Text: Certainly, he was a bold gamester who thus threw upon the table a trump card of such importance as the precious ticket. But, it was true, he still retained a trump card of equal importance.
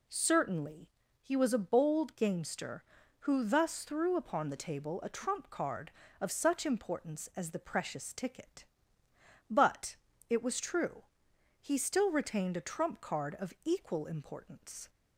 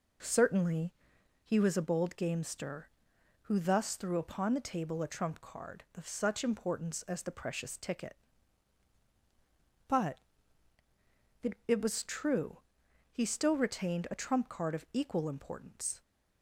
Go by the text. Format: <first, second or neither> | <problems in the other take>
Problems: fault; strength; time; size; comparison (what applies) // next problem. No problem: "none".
first | says "it" twice; at 11.6 s